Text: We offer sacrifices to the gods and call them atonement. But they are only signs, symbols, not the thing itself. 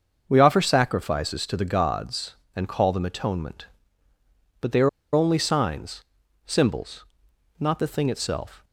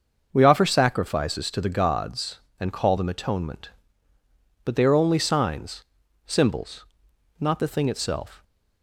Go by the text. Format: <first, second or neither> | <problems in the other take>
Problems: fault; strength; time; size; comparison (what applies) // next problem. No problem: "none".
second | starts louder than the rest; until 1.2 s; 6.5 dB; also in the second // pauses between "are" and "only"; slight; at 4.8 s; 0.24 s long